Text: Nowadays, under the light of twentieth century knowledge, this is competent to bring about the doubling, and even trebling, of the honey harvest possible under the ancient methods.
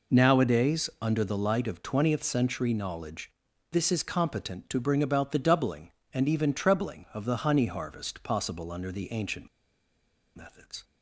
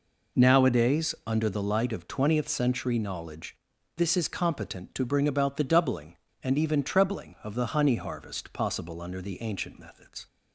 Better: second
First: pauses between "ancient" and "methods"; noticeable; at 9.4 s; 0.87 s long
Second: none

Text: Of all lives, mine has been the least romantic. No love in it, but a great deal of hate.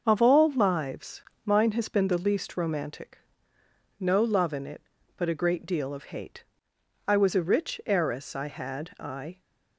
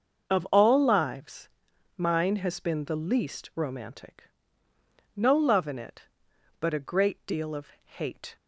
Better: second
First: starts louder than the rest; until 1.0 s; 6 dB // goes on to say "I was a rich heiress I had I"; strong; from 7.0 s on; 2.3 s long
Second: starts louder than the rest; until 1.3 s; 6.5 dB

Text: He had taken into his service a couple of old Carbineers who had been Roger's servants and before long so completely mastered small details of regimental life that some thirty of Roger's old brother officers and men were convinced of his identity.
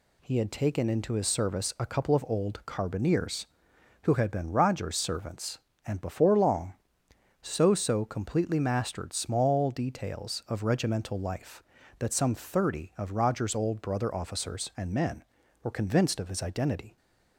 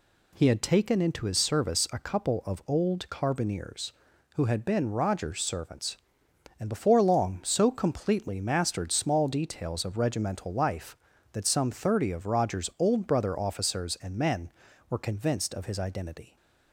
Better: second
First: says "so" twice; at 7.7 s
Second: none

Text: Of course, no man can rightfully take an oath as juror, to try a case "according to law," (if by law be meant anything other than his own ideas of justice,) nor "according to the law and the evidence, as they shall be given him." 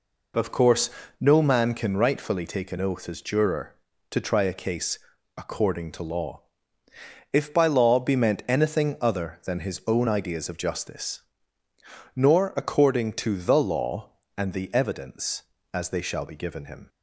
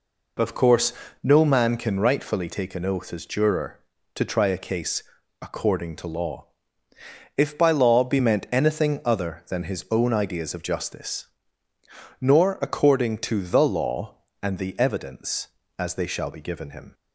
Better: neither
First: pauses between "case" and "according"; at 4.9 s; 0.40 s long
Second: pauses between "case" and "according"; at 5.0 s; 0.40 s long

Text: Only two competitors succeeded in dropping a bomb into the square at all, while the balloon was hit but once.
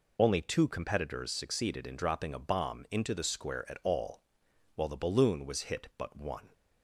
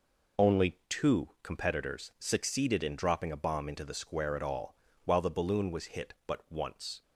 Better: second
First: says "one" for "once"; at 6.1 s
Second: none

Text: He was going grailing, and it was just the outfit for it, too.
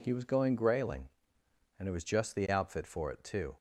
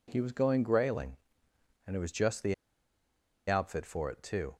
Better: first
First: none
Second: pauses between "the" and "outfit"; noticeable; at 2.5 s; 0.95 s long

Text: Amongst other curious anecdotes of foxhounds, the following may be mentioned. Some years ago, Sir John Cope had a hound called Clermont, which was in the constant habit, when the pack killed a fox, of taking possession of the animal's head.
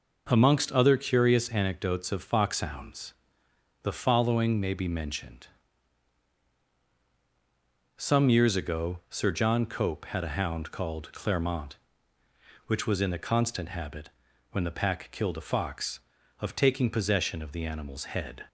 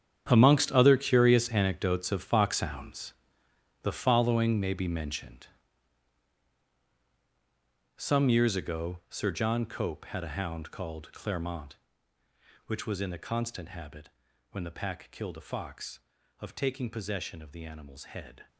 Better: first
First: none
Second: gets quieter; strong; throughout; 14 dB

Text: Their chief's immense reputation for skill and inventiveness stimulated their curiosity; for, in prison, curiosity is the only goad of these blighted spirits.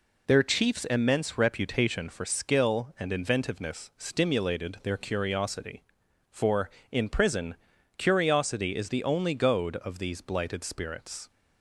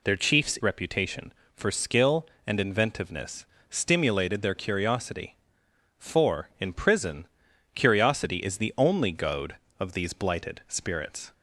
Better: first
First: none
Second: skips "immense"; at 0.5 s // pauses between "inventiveness" and "stimulated"; slight; at 3.4 s; 0.24 s long

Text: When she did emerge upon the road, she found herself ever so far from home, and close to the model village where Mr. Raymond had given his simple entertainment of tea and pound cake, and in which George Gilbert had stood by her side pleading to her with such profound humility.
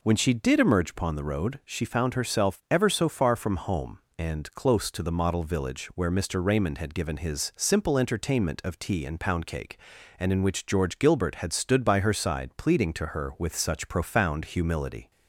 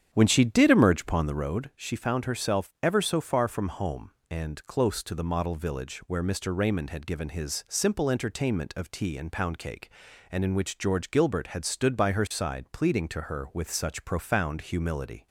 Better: first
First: none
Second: starts louder than the rest; strong; until 1.6 s; 8.5 dB

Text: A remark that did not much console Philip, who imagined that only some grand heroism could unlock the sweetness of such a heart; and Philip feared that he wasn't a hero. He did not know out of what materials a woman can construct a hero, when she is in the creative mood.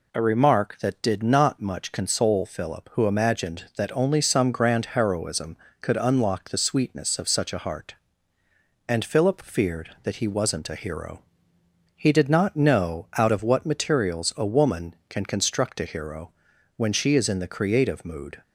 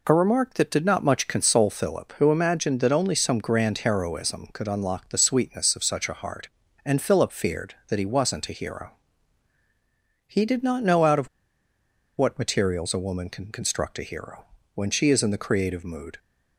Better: first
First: none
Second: pauses between "of" and "what"; noticeable; at 11.2 s; 0.90 s long

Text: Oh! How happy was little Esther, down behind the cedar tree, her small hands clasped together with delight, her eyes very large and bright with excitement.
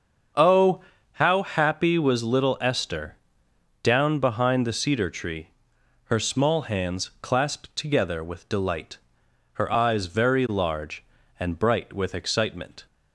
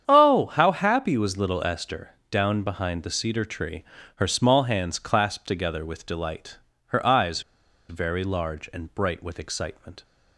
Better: first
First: starts louder than the rest; until 1.6 s; 6.5 dB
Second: starts louder than the rest; strong; until 1.1 s; 8.5 dB // pauses between "eyes" and "very"; noticeable; at 7.4 s; 0.48 s long

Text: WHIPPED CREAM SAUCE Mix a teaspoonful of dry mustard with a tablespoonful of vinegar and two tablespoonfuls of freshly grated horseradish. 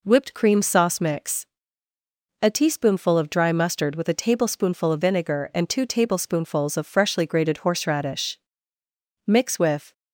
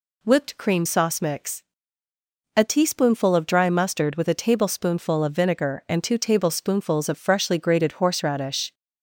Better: second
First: pauses between "Mix" and "a"; noticeable; at 1.4 s; 0.98 s long // goes on to say "Mix with"; noticeable; from 9.2 s on; 0.66 s long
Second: pauses between "Mix" and "a"; noticeable; at 1.6 s; 0.92 s long

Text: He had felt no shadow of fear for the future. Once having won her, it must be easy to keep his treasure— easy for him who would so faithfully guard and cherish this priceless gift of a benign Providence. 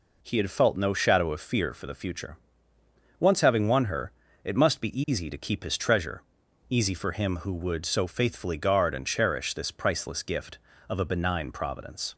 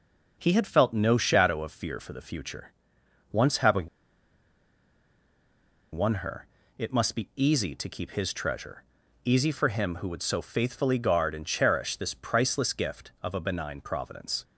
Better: first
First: none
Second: pauses between "having" and "won"; strong; at 3.8 s; 2.0 s long

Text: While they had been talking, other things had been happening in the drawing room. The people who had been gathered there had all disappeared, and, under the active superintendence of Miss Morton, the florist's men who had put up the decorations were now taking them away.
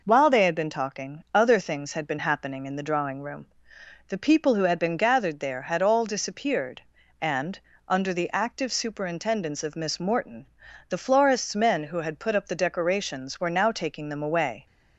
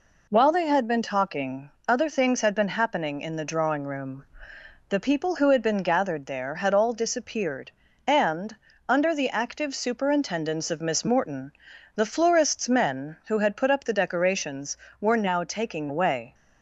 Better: first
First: none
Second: skips "them"; at 15.8 s

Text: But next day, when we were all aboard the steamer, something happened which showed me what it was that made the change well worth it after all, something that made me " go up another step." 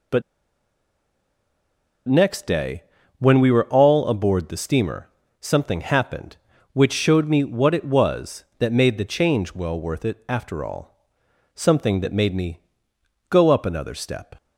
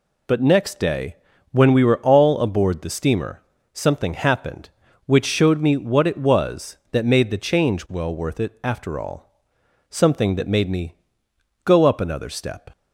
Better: second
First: pauses between "But" and "next"; strong; at 0.2 s; 1.8 s long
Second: none

